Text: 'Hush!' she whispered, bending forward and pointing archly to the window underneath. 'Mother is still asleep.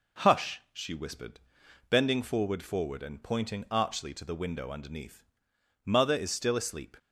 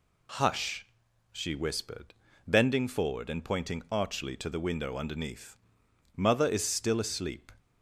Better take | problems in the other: second | says "forward" twice; at 2.6 s

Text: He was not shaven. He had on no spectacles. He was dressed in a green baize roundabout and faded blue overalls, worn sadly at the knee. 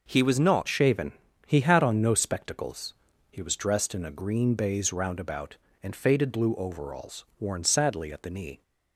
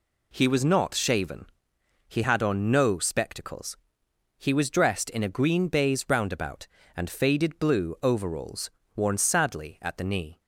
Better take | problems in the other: second | changes voice at "shaven"; from 0.6 s on; 8.0 s long

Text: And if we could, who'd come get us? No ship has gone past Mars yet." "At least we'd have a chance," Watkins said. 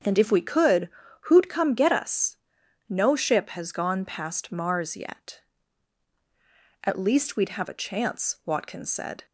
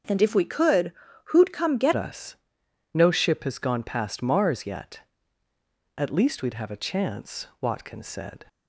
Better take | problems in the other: first | starts louder than the rest; strong; until 1.4 s; 7.5 dB; strong in the first // changes voice at "us"; from 1.9 s on; 6.5 s long

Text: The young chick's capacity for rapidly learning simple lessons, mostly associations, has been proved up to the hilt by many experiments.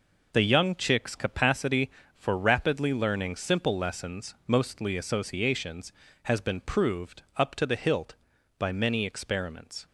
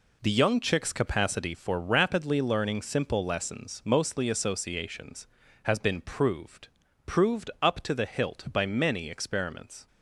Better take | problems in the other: first | says "proved" twice; at 7.0 s

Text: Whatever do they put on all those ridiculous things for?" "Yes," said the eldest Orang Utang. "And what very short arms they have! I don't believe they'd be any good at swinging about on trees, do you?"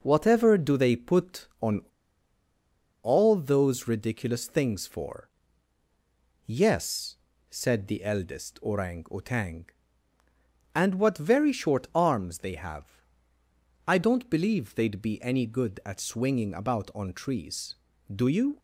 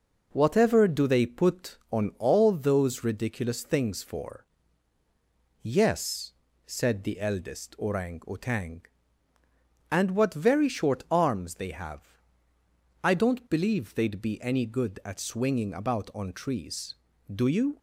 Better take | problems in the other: second | pauses between "on" and "all"; at 1.8 s; 1.2 s long

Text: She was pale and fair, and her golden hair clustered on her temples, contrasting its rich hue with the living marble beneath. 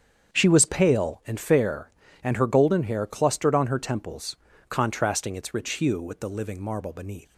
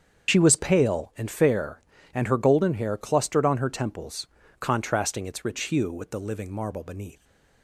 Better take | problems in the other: first | loses the start of "She"; at 0.2 s; 45 ms // starts louder than the rest; strong; until 1.3 s; 7.5 dB; strong in the first

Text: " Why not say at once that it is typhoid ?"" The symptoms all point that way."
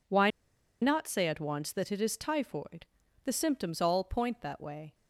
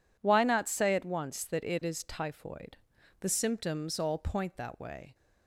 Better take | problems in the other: second | pauses between "Why" and "not"; noticeable; at 0.3 s; 0.51 s long

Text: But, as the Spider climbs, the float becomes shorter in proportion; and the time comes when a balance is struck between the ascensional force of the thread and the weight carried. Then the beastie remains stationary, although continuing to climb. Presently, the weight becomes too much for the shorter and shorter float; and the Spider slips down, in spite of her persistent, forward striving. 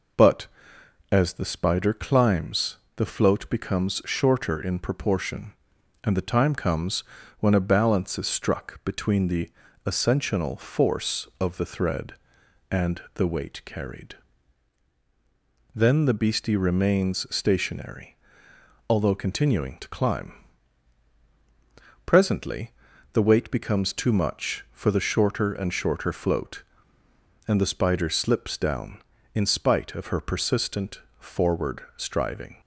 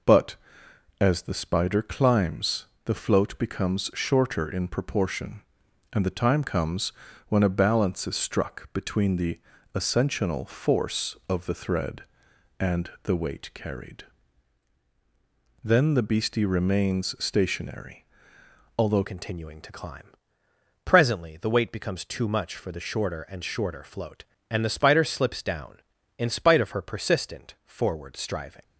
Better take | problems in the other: first | pauses between "comes" and "when"; slight; at 6.9 s; 0.36 s long; slight in the first // pauses between "the" and "ascensional"; at 9.3 s; 0.38 s long; also in the first // changes voice at "continuing"; from 19.0 s on; 9.6 s long

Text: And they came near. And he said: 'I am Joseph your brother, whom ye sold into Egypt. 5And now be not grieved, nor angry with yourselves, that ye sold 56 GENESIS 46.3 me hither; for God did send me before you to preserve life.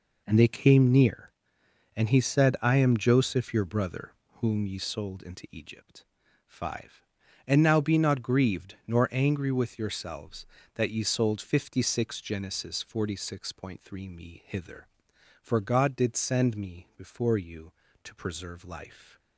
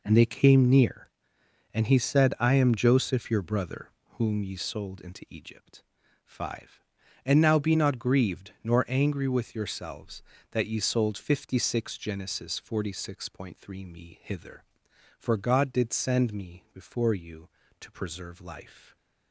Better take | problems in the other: neither | none

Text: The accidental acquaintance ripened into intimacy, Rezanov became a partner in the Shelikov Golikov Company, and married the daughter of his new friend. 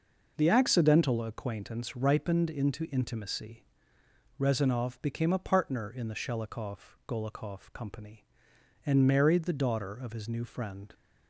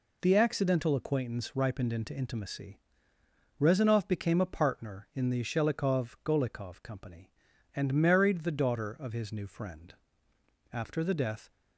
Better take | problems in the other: first | goes on to say "After the death"; noticeable; from 10.7 s on; 0.78 s long

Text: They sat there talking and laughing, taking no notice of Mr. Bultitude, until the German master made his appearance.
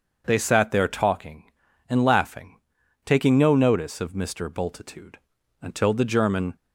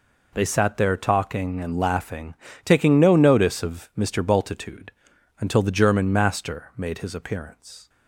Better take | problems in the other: second | starts louder than the rest; until 1.2 s; 6.5 dB // stops before "master made his appearance"; at 6.5 s

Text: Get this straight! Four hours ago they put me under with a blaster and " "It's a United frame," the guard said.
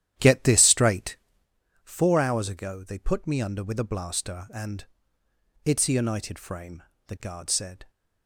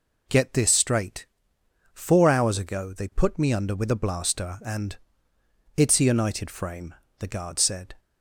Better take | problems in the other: second | starts louder than the rest; strong; until 1.5 s; 11.5 dB

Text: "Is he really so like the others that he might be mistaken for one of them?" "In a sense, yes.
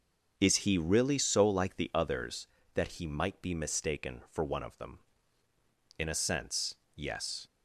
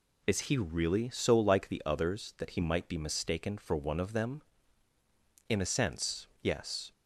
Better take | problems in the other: neither | none

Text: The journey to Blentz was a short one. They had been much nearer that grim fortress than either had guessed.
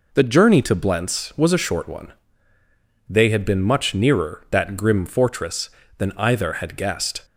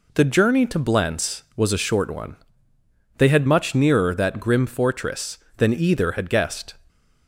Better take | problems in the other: first | skips "been"; at 3.4 s

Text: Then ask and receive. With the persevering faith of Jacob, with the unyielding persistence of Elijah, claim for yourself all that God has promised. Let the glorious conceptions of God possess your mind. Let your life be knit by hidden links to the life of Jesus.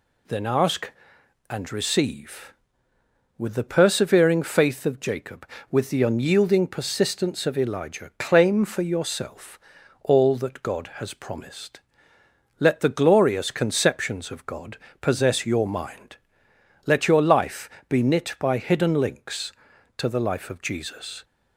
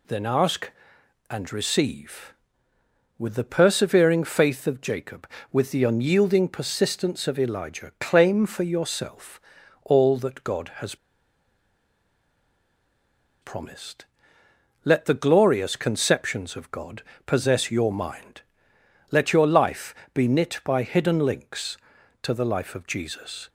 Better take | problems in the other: first | pauses between "yourself" and "all"; at 9.4 s; 0.42 s long; also in the first // pauses between "has" and "promised"; strong; at 10.9 s; 2.4 s long // pauses between "God" and "possess"; slight; at 17.0 s; 0.24 s long; slight in the first // pauses between "life" and "be"; slight; at 19.9 s; 0.22 s long; slight in the first

